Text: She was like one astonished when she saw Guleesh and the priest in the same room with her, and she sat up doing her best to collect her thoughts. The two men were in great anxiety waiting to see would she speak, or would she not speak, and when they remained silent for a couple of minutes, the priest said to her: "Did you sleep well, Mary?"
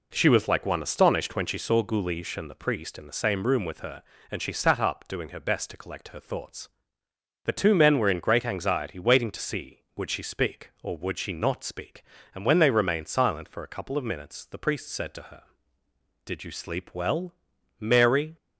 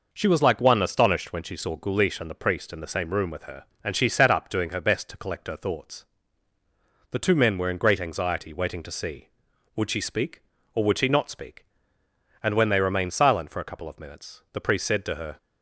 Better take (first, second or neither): first